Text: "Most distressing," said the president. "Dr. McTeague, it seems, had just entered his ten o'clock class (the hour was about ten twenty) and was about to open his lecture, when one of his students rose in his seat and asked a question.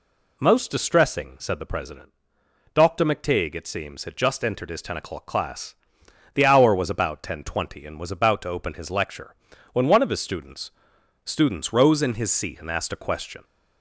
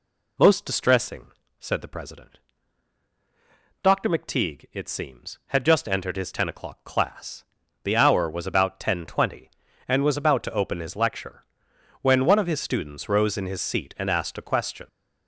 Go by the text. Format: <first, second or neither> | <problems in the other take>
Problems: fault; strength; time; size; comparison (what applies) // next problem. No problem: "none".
second | says "students" twice; at 11.2 s